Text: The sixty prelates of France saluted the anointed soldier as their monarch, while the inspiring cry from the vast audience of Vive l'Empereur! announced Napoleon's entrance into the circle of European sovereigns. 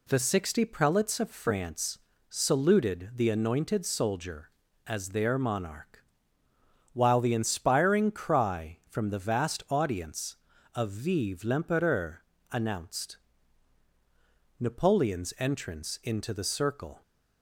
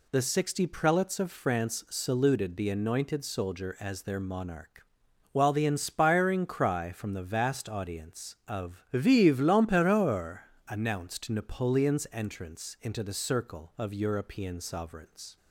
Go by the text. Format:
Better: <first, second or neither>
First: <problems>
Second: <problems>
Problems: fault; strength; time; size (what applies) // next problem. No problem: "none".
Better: second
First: pauses between "France" and "saluted"; slight; at 1.9 s; 0.32 s long // pauses between "announced" and "Napoleon's"; strong; at 13.1 s; 1.4 s long // stops before "of European sovereigns"; at 17.0 s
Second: none